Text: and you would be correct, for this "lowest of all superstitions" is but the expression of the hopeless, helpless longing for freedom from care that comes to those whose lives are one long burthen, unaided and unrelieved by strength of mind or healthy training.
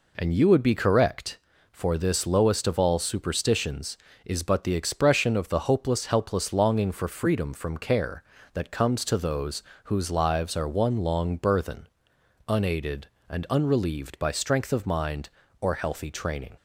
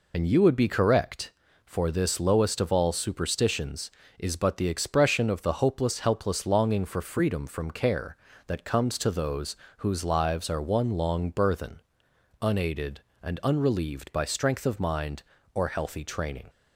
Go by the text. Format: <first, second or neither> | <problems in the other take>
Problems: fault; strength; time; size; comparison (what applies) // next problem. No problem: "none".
first | loses the start of "and"; at 0.1 s; 60 ms // pauses between "those" and "whose"; slight; at 9.5 s; 0.22 s long; slight in the first